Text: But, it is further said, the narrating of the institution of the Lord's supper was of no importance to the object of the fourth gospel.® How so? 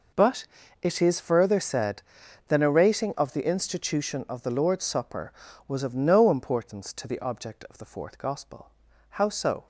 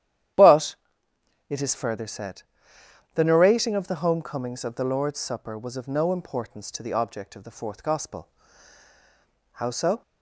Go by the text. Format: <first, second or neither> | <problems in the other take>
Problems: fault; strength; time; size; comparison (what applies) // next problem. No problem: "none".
first | starts louder than the rest; strong; until 2.1 s; 11 dB // says "homecomings" for "institution"; at 3.9 s